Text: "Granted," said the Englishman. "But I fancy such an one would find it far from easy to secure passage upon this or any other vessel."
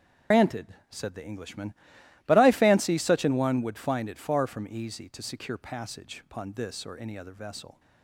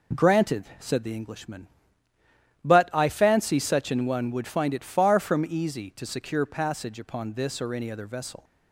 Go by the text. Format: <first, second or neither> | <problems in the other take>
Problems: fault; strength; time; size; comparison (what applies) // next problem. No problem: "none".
second | loses the start of "Granted"; at 0.3 s; 145 ms // starts louder than the rest; strong; until 1.4 s; 8 dB